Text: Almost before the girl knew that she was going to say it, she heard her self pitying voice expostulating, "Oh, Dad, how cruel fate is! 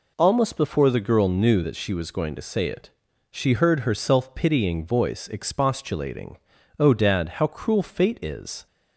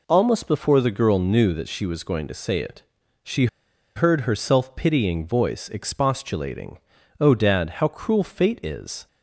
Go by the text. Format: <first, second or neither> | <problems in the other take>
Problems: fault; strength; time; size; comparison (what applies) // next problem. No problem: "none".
first | pauses between "she" and "heard"; noticeable; at 3.4 s; 0.49 s long